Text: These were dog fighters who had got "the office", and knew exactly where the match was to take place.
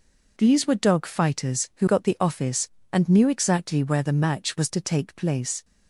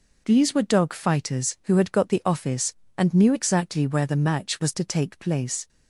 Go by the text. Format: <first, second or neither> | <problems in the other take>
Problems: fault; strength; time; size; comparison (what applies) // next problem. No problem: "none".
second | skips "had"; at 1.8 s